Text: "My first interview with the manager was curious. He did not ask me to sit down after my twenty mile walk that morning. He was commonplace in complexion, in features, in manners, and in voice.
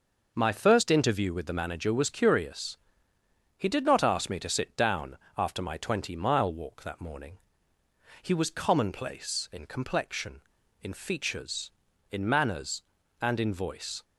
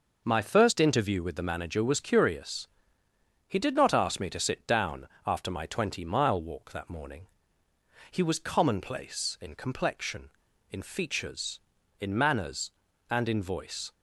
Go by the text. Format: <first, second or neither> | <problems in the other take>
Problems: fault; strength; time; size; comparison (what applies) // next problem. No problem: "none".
neither | pauses between "down" and "after"; slight; the same in both